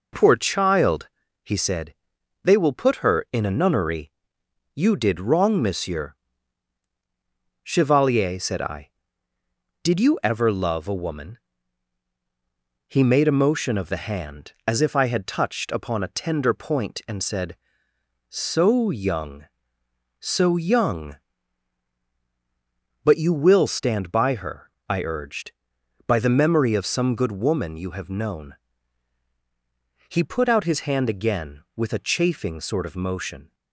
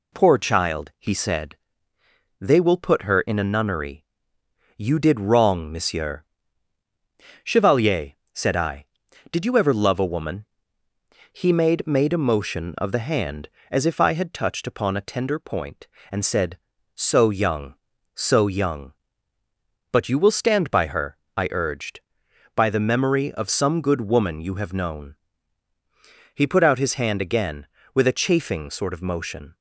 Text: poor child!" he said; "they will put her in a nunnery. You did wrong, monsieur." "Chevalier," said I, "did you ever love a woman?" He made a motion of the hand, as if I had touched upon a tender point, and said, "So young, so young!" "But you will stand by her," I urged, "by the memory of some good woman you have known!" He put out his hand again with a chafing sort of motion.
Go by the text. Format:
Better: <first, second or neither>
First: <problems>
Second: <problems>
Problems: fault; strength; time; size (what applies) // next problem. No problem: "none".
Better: first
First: none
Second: says "made" twice; at 11.8 s